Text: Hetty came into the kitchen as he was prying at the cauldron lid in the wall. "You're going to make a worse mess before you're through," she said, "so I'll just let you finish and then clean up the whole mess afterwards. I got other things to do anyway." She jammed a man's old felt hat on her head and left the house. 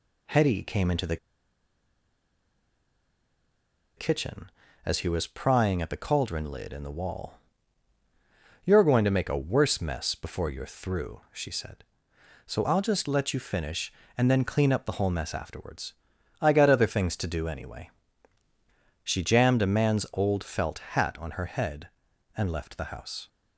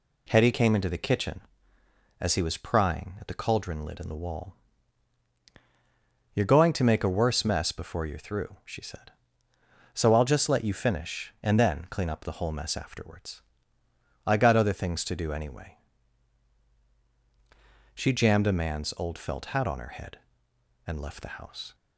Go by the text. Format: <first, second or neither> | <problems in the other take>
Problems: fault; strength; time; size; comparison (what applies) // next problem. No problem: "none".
second | pauses between "the" and "kitchen"; strong; at 1.1 s; 2.8 s long